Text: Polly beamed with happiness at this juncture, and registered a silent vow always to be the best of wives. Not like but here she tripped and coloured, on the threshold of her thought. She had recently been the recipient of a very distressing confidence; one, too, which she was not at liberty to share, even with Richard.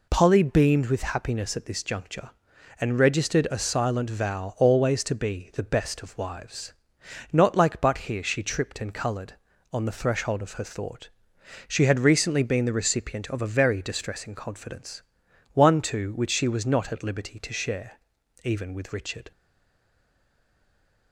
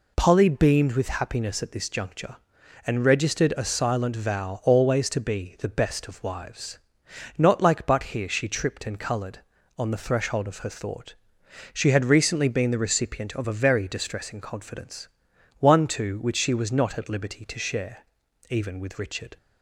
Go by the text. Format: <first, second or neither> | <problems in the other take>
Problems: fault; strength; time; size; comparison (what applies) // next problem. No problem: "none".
second | stays silent after the last word; noticeable; from 19.3 s on; 1.8 s long